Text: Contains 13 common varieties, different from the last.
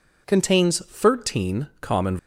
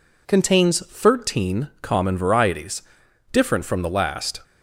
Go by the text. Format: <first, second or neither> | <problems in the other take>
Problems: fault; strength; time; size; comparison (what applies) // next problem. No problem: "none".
second | stops before "varieties different from the last"; at 2.1 s